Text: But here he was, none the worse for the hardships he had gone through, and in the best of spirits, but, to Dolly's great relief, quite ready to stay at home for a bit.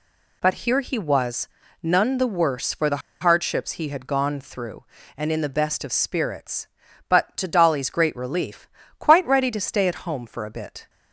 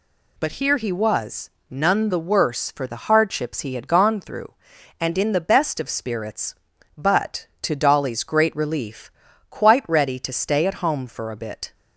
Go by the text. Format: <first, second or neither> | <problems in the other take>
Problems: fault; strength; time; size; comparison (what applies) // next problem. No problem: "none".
second | pauses between "the" and "hardships"; slight; at 3.0 s; 0.22 s long